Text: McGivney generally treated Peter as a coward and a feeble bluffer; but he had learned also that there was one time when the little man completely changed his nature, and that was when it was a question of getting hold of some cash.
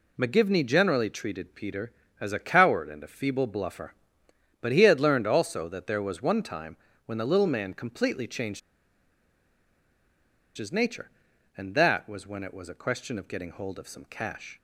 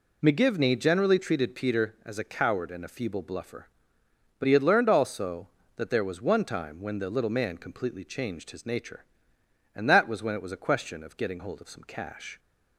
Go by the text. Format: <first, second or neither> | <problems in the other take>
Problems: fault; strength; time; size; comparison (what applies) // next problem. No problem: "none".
second | pauses between "time" and "when"; slight; at 6.7 s; 0.30 s long // pauses between "changed" and "his"; strong; at 8.5 s; 1.9 s long